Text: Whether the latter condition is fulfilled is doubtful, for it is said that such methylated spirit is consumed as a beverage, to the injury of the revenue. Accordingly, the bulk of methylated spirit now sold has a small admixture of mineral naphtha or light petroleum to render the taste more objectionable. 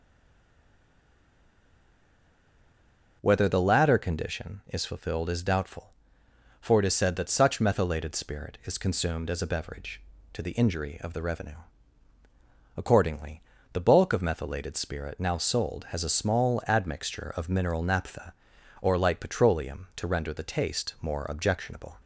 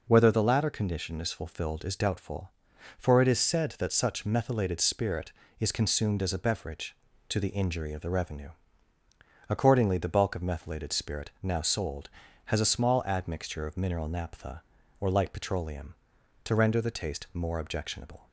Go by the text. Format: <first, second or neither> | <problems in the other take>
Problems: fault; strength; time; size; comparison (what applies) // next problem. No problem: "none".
second | stays silent before the first word; strong; until 3.2 s; 3.2 s long // starts louder than the rest; until 4.2 s; 6 dB